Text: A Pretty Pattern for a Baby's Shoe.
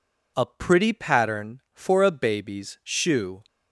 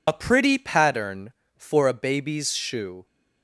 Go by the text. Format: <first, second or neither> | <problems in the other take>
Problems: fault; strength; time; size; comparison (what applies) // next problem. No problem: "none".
first | loses the start of "A"; at 0.0 s; 55 ms